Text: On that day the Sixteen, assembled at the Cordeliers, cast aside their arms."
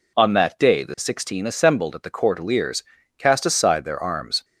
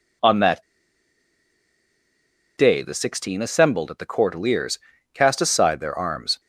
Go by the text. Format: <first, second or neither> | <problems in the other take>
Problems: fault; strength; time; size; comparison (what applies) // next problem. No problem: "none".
first | pauses between "that" and "day"; strong; at 0.6 s; 1.9 s long